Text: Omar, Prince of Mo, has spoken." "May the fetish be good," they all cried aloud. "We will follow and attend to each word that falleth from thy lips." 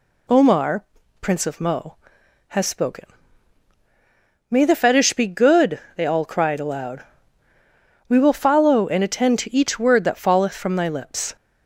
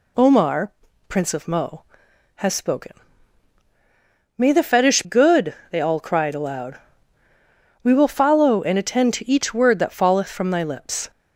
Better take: first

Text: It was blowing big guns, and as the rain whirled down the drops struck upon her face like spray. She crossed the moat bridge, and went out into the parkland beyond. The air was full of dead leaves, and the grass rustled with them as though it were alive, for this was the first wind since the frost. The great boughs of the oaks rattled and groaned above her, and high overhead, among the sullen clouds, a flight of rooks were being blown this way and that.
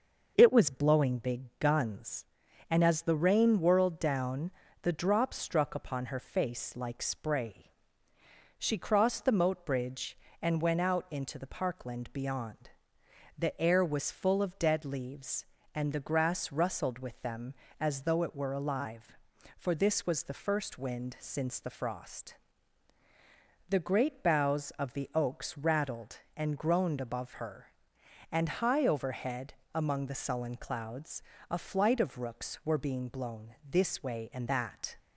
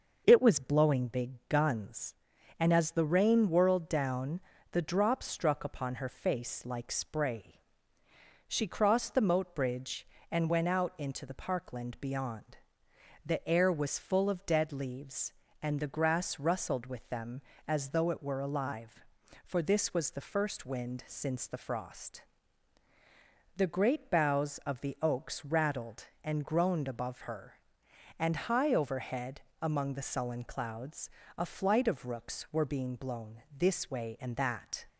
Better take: neither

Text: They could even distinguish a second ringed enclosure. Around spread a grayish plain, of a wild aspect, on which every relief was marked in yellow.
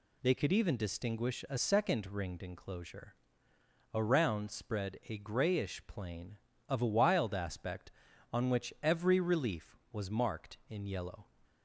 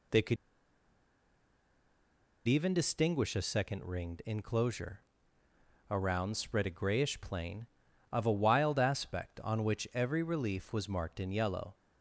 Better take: first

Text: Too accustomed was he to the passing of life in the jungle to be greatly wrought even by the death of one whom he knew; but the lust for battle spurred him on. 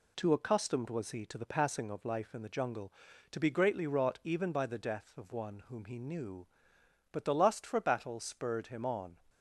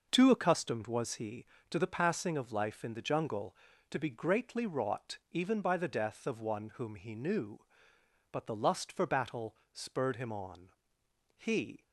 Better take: first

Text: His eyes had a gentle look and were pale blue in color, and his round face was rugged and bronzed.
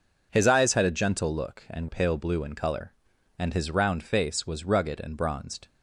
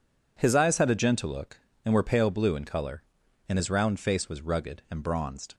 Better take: second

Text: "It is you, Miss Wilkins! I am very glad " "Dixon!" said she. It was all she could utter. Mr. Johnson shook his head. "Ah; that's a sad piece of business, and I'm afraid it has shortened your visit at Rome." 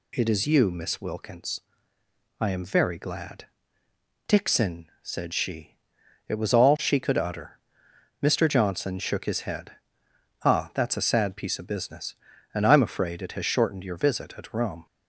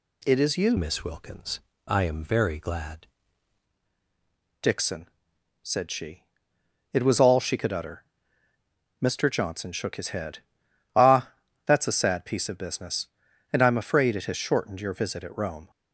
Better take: first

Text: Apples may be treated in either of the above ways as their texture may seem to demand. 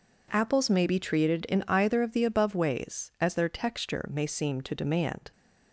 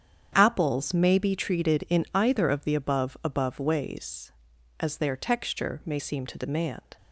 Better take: first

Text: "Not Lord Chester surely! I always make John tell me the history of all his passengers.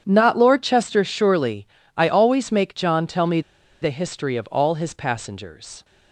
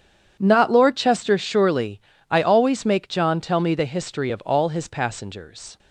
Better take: second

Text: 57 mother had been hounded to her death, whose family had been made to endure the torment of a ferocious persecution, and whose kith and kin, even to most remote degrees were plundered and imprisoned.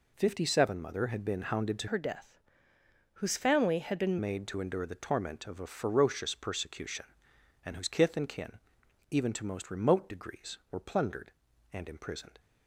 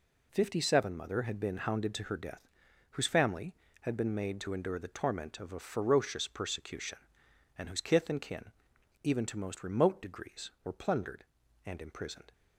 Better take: second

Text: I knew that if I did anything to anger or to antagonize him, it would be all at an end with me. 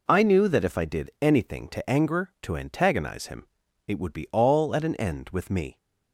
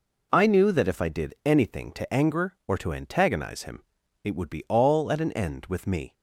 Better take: second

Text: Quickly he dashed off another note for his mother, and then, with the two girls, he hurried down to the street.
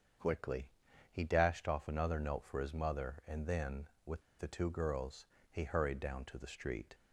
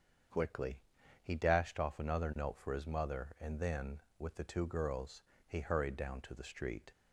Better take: second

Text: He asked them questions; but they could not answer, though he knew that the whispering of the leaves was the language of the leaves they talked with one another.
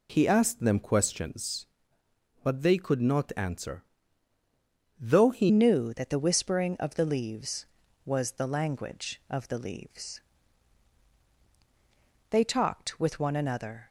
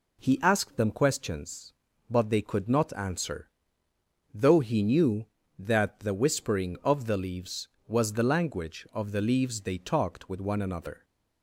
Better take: second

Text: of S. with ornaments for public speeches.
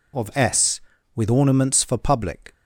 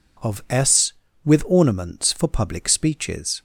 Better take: second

